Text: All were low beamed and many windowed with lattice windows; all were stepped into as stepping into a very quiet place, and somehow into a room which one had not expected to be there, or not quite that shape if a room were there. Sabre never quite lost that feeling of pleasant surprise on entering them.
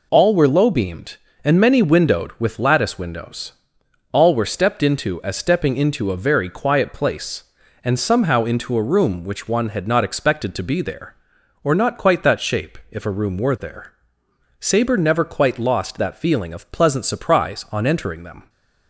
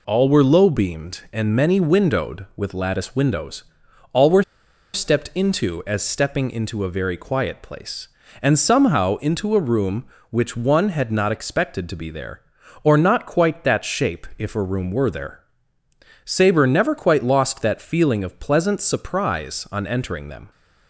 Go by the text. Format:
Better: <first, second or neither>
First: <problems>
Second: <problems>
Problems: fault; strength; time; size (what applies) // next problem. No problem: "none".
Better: first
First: none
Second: pauses between "were" and "stepped"; noticeable; at 4.4 s; 0.51 s long